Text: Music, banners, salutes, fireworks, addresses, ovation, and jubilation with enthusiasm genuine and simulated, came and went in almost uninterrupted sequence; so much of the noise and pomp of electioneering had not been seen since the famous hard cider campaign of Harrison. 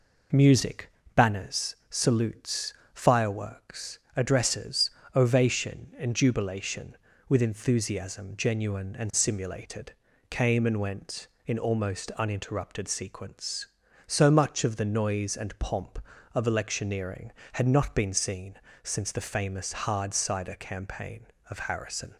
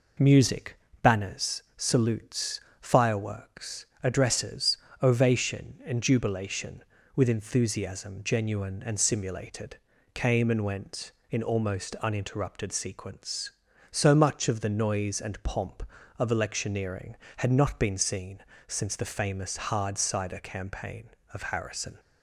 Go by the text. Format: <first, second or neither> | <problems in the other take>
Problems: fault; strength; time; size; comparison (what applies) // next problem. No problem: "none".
neither | pauses between "seen" and "since"; slight; the same in both